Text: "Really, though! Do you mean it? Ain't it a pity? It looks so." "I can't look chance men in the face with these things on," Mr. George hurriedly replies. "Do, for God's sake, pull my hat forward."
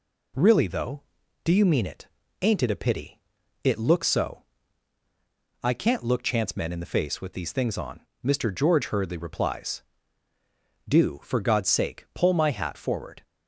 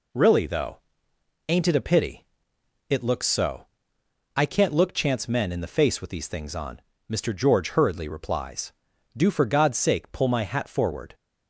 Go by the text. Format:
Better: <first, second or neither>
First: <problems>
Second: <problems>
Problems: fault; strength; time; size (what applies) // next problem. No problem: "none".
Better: first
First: none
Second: skips "Do you mean it"; at 1.1 s